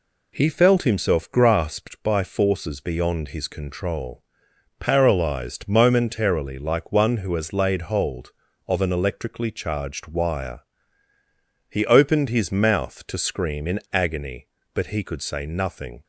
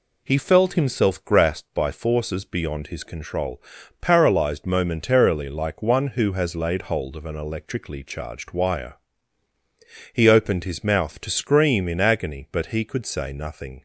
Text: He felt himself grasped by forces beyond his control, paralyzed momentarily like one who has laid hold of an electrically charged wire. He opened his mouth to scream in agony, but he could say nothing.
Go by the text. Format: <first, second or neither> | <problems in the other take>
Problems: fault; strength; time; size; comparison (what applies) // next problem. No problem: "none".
neither | none